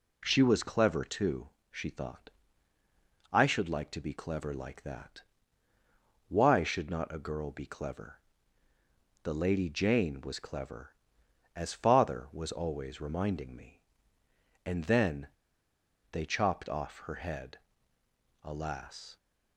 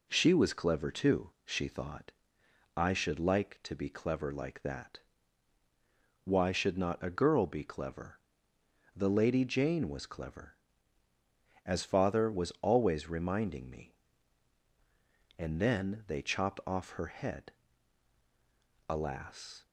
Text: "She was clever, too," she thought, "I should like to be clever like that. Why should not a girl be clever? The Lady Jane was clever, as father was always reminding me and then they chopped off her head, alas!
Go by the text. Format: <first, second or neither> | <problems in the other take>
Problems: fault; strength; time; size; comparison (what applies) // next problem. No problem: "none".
second | pauses between "then" and "they"; noticeable; at 15.2 s; 0.82 s long